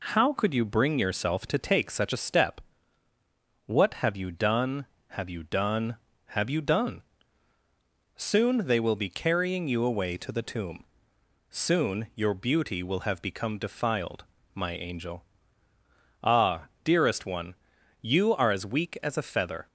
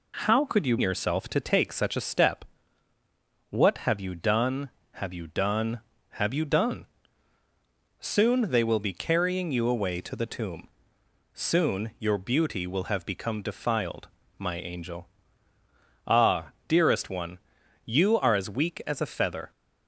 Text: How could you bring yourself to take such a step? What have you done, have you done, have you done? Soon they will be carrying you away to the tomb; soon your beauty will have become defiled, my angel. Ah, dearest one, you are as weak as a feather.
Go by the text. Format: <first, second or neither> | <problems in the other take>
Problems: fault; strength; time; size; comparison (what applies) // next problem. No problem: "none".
first | skips "bring"; at 0.7 s